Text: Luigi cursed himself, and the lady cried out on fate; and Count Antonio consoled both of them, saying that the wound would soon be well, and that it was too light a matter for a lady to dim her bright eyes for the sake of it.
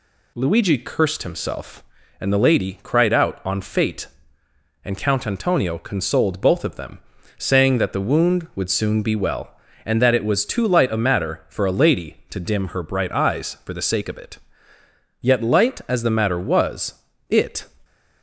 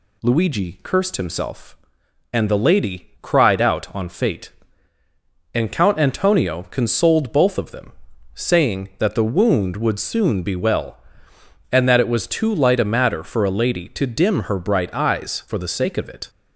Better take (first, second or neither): second